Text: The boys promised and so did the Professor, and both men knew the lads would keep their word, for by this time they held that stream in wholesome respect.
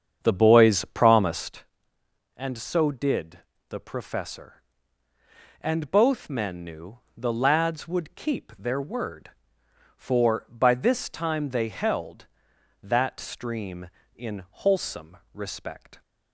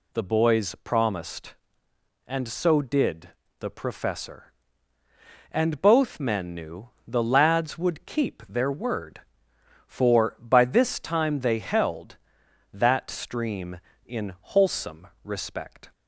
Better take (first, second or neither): second